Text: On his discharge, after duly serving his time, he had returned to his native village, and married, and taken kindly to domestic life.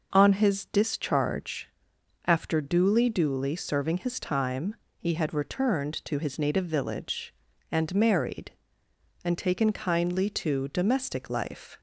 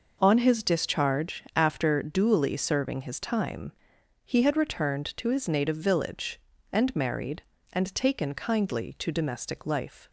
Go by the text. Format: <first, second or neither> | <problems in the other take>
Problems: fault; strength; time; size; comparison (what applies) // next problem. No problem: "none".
second | says "duly" twice; at 3.0 s